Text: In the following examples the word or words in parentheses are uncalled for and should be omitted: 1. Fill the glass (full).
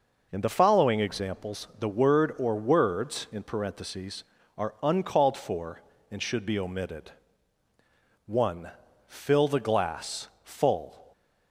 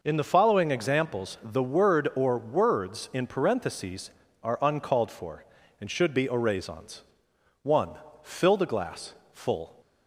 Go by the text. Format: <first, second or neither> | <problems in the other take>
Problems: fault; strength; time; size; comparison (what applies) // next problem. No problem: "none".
first | says "oraisons" for "omitted"; at 6.2 s